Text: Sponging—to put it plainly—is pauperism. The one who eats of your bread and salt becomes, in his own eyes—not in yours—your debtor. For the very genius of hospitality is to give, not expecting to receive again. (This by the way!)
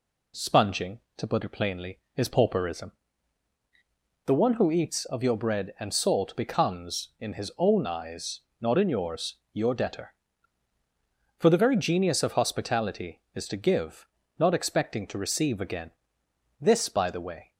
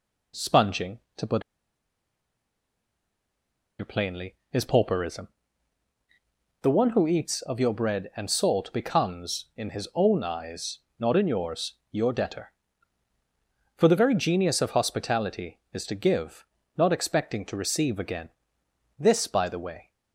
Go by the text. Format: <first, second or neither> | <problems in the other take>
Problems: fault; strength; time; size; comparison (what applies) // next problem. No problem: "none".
first | pauses between "put" and "it"; strong; at 1.4 s; 2.3 s long